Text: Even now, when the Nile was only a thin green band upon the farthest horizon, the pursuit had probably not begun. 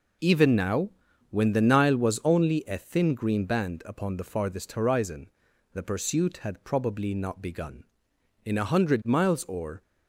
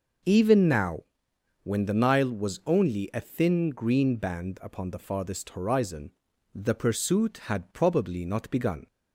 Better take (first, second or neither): second